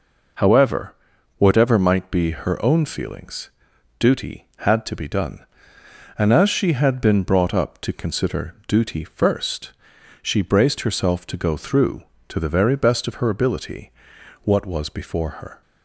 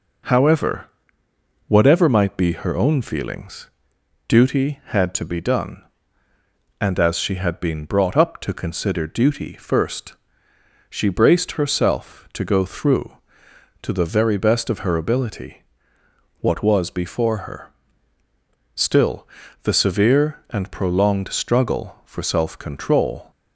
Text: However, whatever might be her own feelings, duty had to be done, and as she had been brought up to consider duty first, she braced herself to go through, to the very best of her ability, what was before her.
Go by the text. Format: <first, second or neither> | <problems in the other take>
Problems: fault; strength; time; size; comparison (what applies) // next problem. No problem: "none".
first | goes on to say "Still the severe and prolonged struggle for self control"; strong; from 18.7 s on; 4.5 s long